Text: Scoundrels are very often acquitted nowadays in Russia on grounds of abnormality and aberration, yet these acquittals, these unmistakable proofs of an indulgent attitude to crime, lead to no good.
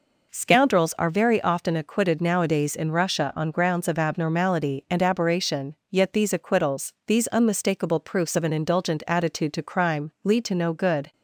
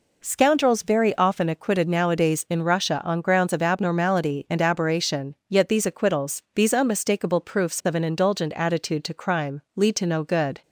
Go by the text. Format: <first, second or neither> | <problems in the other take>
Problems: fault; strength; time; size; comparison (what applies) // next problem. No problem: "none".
first | skips "are"; at 0.8 s